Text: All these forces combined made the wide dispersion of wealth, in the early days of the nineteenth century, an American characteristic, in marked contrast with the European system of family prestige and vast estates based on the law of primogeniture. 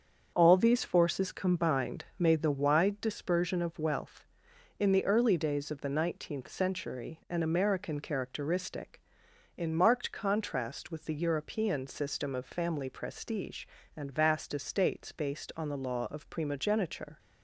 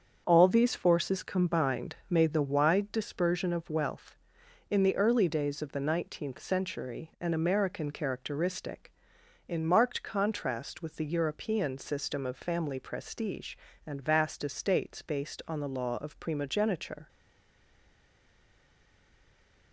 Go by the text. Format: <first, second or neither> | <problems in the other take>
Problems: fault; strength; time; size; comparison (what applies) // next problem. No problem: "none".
first | starts louder than the rest; until 1.2 s; 7 dB; also in the first // stays silent after the last word; strong; from 17.0 s on; 2.7 s long